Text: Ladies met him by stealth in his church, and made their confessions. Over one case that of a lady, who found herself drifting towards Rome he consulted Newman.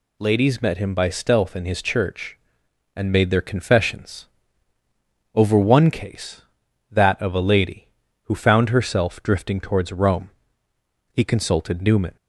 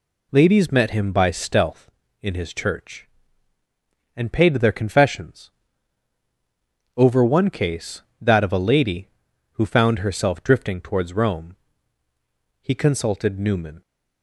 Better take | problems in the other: first | says "paid" for "made"; at 4.3 s // pauses between "Rome" and "he"; at 11.5 s; 1.0 s long; noticeable in the first

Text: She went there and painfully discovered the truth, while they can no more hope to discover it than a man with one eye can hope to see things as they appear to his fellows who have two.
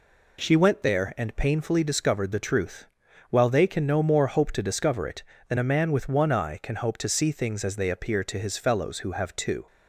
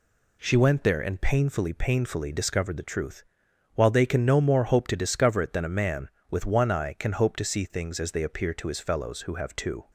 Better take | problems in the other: first | says "painfully" twice; at 1.7 s

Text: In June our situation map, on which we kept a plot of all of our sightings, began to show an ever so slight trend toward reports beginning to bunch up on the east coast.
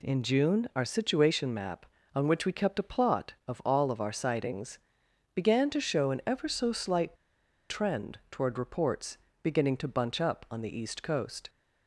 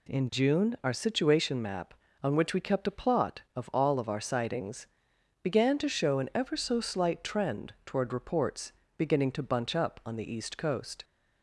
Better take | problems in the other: second | pauses between "slight" and "trend"; noticeable; at 7.1 s; 0.56 s long // pauses between "reports" and "beginning"; slight; at 9.1 s; 0.26 s long; slight in the second

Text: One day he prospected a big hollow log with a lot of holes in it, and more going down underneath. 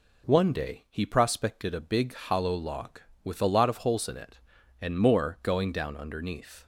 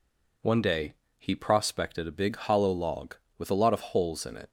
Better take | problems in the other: first | pauses between "day" and "he"; slight; at 0.9 s; 0.24 s long // stops before "and more going down underneath"; at 4.4 s

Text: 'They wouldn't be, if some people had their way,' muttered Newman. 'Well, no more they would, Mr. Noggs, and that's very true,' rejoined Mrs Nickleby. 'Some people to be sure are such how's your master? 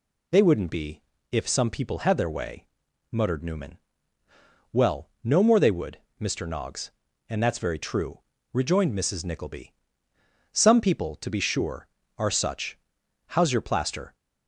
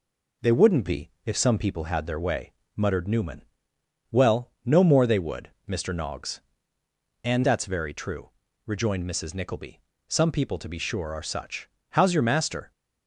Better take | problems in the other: second | pauses between "such" and "how's"; noticeable; at 12.7 s; 0.52 s long; slight in the second // says "plaster" for "master"; at 13.6 s

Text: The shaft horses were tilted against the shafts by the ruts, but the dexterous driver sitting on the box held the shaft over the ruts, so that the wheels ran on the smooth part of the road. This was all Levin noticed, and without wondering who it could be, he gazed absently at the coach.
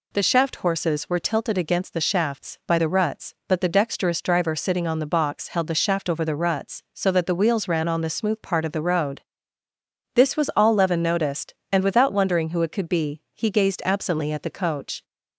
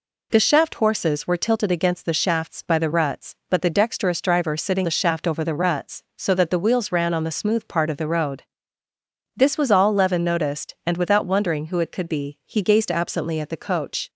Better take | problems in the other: first | skips "on the box held"; at 4.8 s

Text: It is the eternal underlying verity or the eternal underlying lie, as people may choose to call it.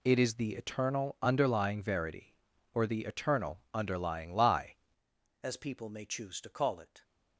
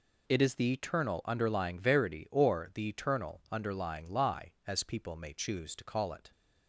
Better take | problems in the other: second | changes voice at "as"; from 5.4 s on; 1.6 s long

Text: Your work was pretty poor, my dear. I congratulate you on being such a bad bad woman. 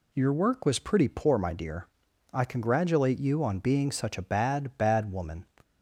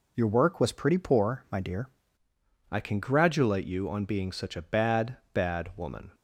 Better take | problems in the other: first | changes voice at "I"; from 2.7 s on; 3.4 s long // pauses between "bad" and "bad"; slight; at 5.1 s; 0.16 s long

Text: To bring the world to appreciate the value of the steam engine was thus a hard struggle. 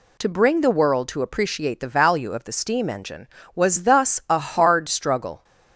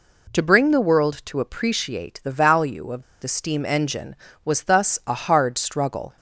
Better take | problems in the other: first | pauses between "of" and "the"; slight; at 3.0 s; 0.19 s long

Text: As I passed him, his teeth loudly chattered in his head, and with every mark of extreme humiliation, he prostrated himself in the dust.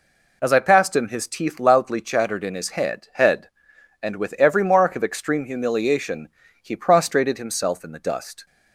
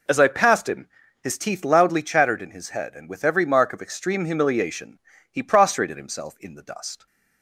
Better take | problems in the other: second | says "head" twice; at 3.1 s

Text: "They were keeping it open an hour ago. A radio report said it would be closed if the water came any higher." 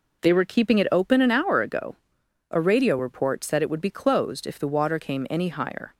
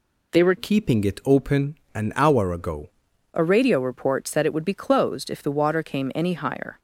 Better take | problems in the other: first | changes voice from "keeping" to "ago"; from 0.5 to 2.8 s; 2.3 s long // pauses between "open" and "an"; slight; at 1.7 s; 0.18 s long

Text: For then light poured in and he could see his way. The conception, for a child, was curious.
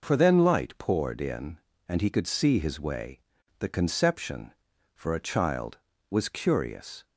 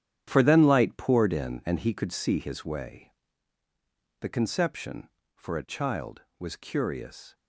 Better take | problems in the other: first | gets quieter; strong; throughout; 11 dB

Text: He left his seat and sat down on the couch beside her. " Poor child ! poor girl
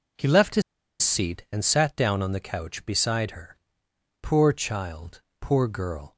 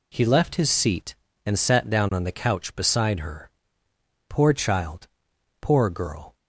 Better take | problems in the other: second | pauses between "his" and "seat"; at 0.6 s; 0.40 s long

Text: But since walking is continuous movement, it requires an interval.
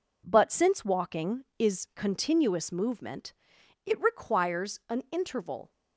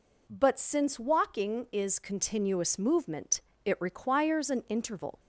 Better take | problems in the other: neither | none

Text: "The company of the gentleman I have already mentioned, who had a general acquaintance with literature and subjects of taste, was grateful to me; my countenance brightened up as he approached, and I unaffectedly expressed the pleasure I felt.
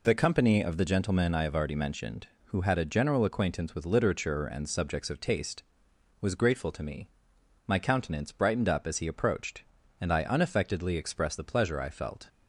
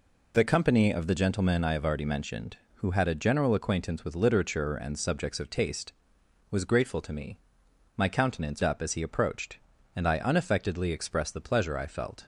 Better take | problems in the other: first | skips "brightened"; at 8.6 s

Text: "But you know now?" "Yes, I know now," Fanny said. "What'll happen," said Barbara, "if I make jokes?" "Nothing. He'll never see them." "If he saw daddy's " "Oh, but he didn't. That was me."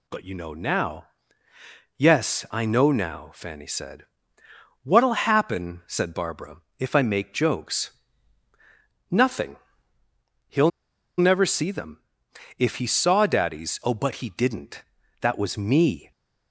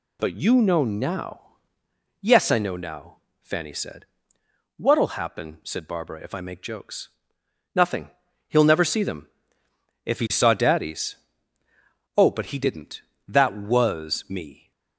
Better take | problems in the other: second | pauses between "He'll" and "never"; noticeable; at 10.7 s; 0.48 s long

